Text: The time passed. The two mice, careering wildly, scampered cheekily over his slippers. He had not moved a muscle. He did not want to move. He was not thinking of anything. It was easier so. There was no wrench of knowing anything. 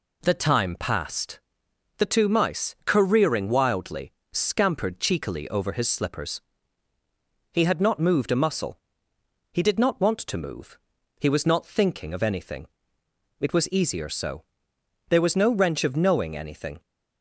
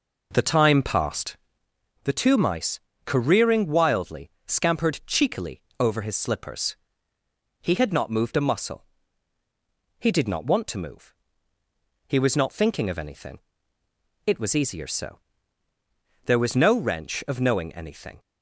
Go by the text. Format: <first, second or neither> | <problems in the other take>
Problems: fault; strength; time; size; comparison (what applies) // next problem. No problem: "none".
first | starts louder than the rest; noticeable; until 1.7 s; 5 dB // pauses between "cheekily" and "over"; slight; at 5.6 s; 0.16 s long